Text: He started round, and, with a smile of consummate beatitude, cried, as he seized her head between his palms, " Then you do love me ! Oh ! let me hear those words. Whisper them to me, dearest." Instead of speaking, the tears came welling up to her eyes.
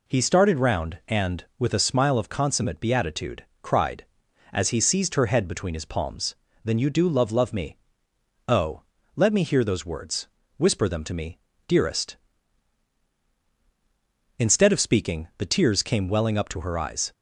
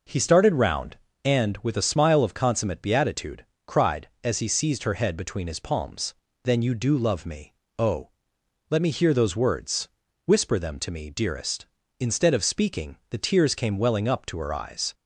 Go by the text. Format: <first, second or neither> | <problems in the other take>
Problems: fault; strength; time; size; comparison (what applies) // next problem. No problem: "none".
second | says "love" twice; at 7.3 s